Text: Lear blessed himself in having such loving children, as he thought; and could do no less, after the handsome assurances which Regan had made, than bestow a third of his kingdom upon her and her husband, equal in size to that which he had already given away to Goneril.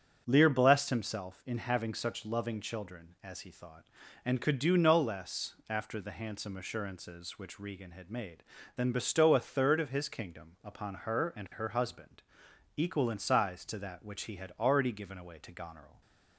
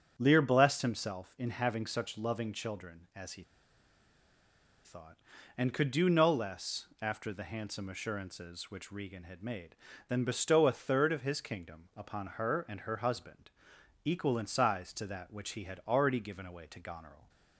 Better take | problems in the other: first | starts louder than the rest; strong; until 1.1 s; 8 dB; strong in the first // pauses between "he" and "thought"; strong; at 3.4 s; 1.4 s long

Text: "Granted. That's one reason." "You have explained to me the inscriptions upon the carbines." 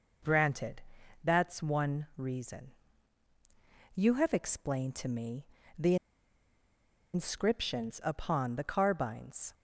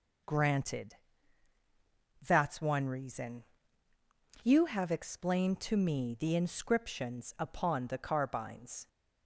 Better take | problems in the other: second | pauses between "me" and "the"; slight; at 5.4 s; 0.34 s long // pauses between "the" and "inscriptions"; at 5.9 s; 1.1 s long

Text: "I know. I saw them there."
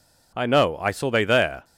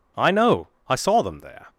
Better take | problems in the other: second | says "they" for "them"; at 1.1 s

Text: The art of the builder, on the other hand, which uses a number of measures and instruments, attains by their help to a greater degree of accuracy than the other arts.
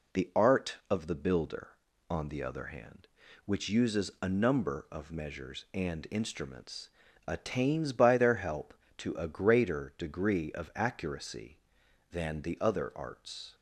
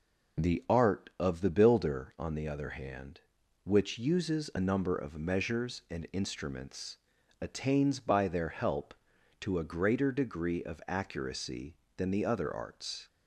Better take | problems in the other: neither | none

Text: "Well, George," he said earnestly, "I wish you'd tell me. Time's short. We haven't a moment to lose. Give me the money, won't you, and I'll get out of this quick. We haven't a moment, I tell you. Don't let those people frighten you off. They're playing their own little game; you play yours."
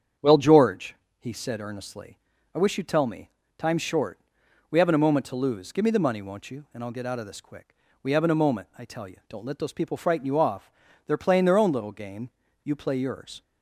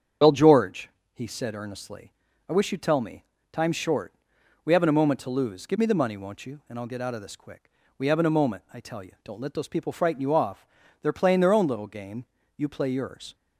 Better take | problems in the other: first | loses the start of "Well"; at 0.2 s; 80 ms // starts louder than the rest; strong; until 1.4 s; 7.5 dB; strong in the first

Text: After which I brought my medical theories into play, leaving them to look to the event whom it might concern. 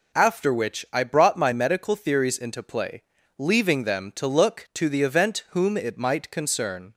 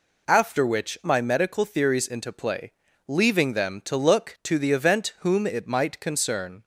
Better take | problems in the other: first | skips "I brought"; at 1.0 s

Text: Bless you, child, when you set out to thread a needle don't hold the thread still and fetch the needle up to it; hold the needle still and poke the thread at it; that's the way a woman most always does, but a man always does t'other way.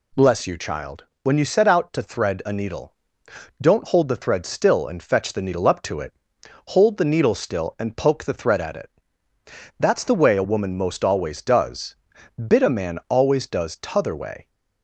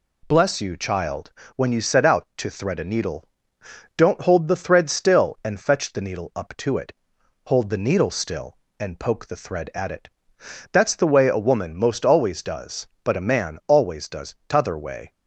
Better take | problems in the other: second | pauses between "needle" and "don't"; noticeable; at 2.9 s; 0.66 s long; noticeable in the second // says "bit" for "but"; at 12.4 s

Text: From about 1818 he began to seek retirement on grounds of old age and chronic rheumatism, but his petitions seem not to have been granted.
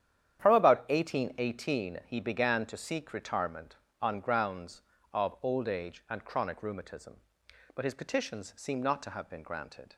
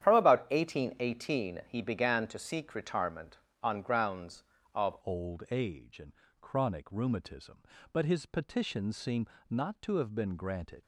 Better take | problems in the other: first | starts louder than the rest; strong; until 1.0 s; 10 dB; strong in the first // changes voice at "old"; from 5.0 s on; 5.8 s long // pauses between "and" and "chronic"; slight; at 6.1 s; 0.30 s long // pauses between "seem" and "not"; slight; at 9.2 s; 0.20 s long

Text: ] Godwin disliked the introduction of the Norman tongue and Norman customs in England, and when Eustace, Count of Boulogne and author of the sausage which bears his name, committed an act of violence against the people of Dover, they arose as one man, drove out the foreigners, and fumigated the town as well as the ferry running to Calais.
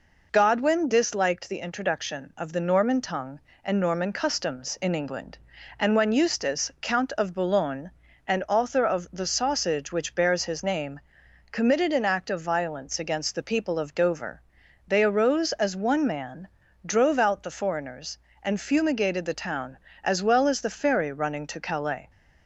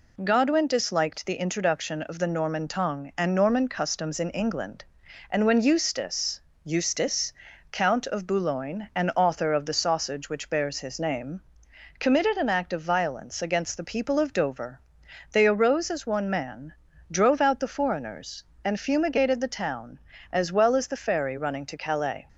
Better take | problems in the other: first | says "Eustace" twice; at 6.6 s

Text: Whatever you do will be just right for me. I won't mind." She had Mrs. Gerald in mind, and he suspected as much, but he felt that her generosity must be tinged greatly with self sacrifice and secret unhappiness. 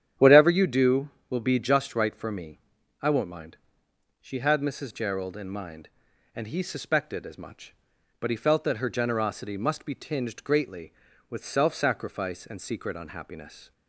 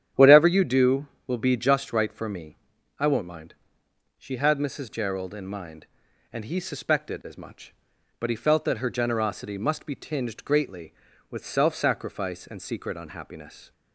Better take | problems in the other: neither | starts louder than the rest; strong; the same in both

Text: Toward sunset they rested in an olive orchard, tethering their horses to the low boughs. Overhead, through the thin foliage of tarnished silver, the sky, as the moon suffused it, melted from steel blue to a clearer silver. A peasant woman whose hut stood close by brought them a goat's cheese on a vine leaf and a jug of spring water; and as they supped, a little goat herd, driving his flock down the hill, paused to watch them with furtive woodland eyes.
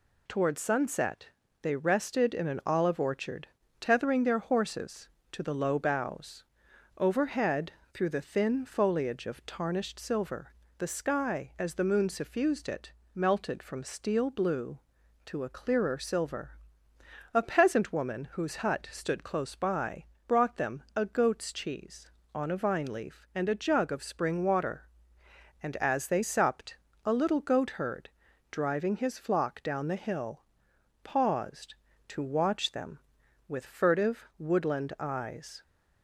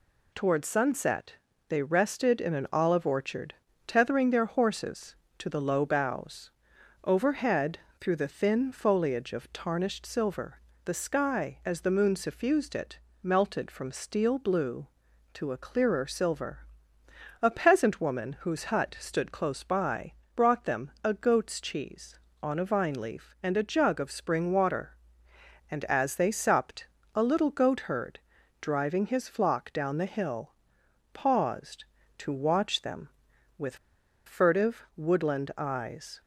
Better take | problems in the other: first | pauses between "sunset" and "they"; slight; at 1.3 s; 0.34 s long; slight in the first // pauses between "by" and "brought"; slight; at 20.1 s; 0.22 s long; slight in the first // pauses between "with" and "furtive"; noticeable; at 33.7 s; 0.49 s long

